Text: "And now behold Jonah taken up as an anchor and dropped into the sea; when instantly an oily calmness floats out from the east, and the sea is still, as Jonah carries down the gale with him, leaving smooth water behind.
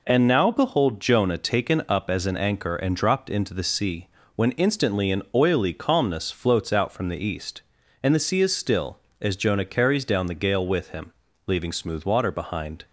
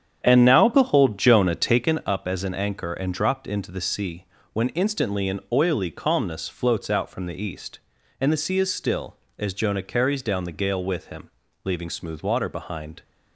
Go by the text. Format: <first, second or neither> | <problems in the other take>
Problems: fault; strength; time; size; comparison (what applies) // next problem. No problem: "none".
first | starts louder than the rest; strong; until 1.9 s; 8.5 dB